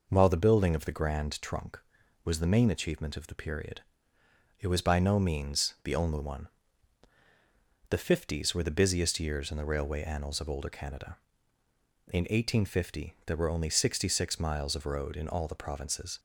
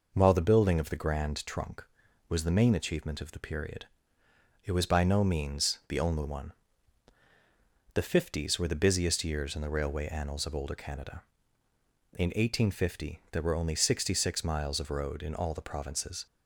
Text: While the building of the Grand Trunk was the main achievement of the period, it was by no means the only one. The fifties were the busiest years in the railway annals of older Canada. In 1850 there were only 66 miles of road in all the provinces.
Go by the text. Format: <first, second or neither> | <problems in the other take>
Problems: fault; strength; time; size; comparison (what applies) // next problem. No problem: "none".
neither | none